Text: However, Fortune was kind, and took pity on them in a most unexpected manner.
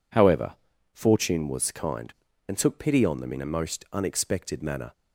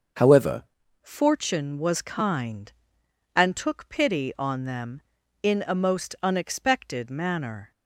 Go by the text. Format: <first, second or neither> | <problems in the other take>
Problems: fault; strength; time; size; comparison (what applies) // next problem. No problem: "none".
first | starts louder than the rest; until 1.5 s; 6.5 dB // changes voice at "Fortune"; from 1.0 s on; 6.7 s long